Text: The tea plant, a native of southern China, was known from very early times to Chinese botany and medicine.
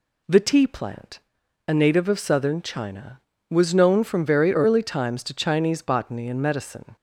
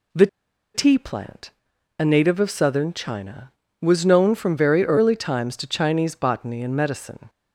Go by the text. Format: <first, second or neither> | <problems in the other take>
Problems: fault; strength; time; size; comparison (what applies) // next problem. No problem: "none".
first | pauses between "The" and "tea"; noticeable; at 0.2 s; 0.47 s long